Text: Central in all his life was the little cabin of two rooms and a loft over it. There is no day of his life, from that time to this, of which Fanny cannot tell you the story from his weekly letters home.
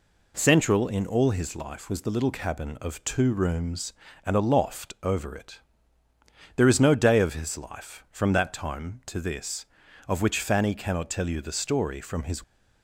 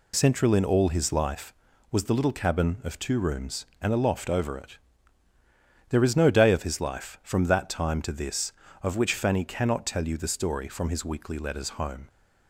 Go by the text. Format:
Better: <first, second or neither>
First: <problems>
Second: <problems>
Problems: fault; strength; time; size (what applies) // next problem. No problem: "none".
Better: second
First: stops before "weekly letters home"; at 12.4 s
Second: none